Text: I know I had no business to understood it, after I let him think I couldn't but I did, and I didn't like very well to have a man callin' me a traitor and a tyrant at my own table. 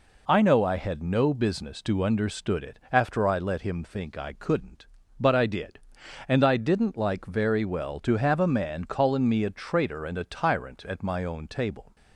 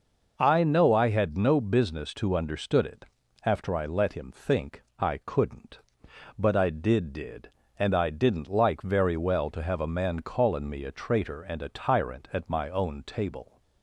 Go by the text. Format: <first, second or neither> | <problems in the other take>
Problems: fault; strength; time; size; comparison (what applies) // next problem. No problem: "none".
first | pauses between "think" and "I"; slight; at 4.8 s; 0.16 s long // says "did" twice; at 7.1 s